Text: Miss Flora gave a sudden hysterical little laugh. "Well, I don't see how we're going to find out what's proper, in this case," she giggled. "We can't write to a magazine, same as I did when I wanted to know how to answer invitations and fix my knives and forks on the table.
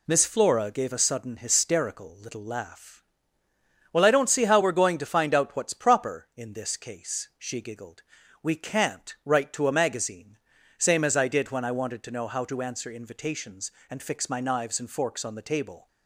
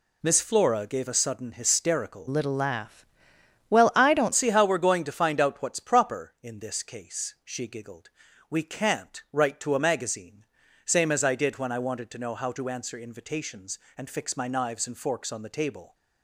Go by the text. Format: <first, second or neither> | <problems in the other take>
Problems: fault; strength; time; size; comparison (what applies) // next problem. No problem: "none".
first | changes voice from "little" to "don't"; from 2.2 to 4.3 s; 2.1 s long